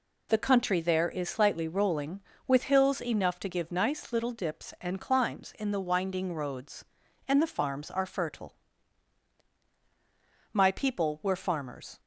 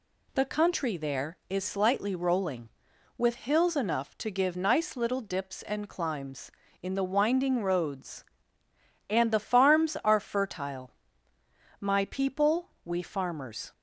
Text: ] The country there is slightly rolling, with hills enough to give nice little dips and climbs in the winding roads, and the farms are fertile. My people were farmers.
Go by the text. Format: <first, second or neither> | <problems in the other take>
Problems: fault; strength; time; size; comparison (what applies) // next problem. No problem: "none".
first | says "we" for "were"; at 12.8 s